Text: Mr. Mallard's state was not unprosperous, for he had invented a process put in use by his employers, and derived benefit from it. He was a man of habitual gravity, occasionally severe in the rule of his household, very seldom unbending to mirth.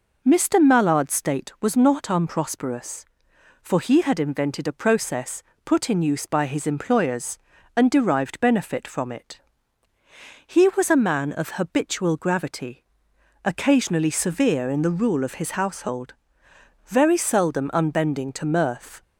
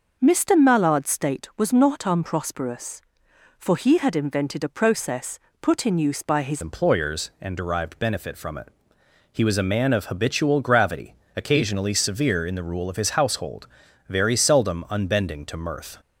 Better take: first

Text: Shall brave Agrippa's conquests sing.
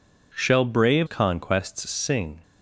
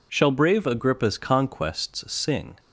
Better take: second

